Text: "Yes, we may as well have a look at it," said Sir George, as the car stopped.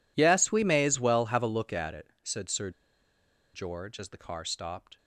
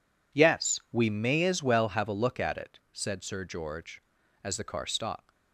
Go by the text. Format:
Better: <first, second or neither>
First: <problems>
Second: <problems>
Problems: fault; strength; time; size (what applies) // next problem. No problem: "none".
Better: second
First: pauses between "Sir" and "George"; noticeable; at 2.7 s; 0.83 s long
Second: none